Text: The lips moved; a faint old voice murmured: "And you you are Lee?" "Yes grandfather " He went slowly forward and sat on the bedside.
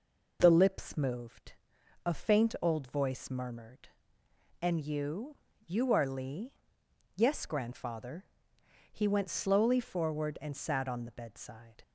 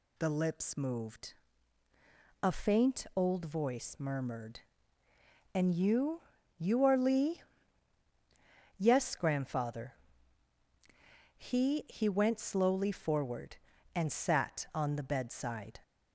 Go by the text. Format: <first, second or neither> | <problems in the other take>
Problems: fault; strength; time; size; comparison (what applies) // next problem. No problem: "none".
first | pauses between "you" and "you"; slight; at 6.2 s; 0.34 s long; slight in the first // says "He" twice; at 11.8 s